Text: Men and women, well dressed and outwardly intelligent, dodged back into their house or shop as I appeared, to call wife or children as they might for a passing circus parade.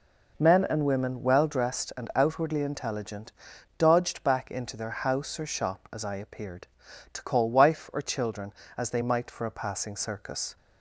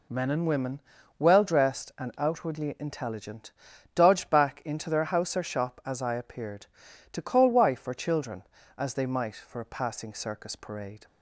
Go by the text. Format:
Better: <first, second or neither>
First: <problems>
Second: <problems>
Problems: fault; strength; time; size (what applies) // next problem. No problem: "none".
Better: second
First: stops before "parade"; at 10.5 s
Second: none